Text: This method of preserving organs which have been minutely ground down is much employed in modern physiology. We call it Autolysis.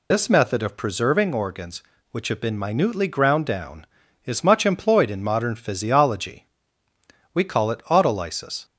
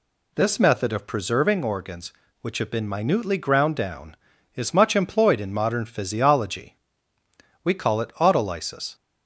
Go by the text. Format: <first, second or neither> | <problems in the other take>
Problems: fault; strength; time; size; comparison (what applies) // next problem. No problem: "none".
second | loses the start of "This"; at 0.1 s; 55 ms